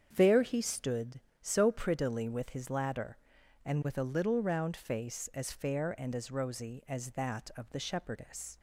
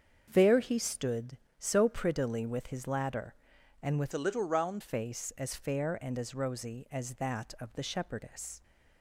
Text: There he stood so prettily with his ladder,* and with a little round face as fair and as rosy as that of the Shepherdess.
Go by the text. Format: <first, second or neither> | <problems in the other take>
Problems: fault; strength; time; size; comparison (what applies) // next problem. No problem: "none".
first | starts louder than the rest; strong; until 1.3 s; 7 dB; strong in the first // changes voice from "a" to "round"; from 4.1 to 4.8 s; 0.7 s long